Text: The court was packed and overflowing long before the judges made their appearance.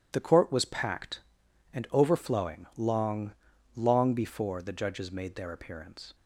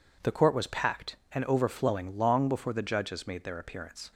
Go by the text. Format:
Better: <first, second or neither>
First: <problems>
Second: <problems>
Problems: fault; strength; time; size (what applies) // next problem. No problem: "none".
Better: second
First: says "long" twice; at 3.7 s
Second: none